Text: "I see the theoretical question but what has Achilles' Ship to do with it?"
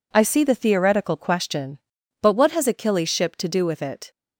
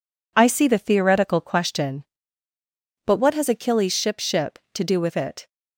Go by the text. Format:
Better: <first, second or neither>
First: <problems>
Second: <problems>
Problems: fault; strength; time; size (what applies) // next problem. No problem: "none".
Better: first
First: none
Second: says "Ship" twice; at 4.1 s